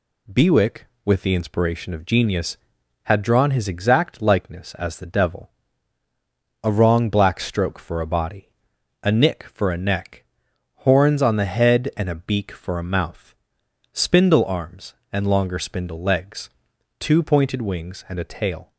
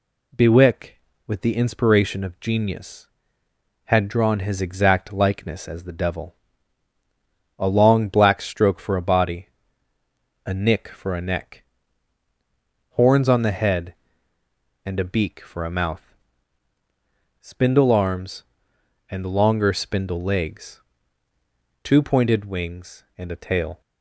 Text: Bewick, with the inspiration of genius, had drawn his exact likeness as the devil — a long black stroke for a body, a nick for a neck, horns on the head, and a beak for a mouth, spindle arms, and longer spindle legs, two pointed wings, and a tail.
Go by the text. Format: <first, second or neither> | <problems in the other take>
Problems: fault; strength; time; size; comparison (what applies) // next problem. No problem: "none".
second | says "wrong" for "long"; at 6.7 s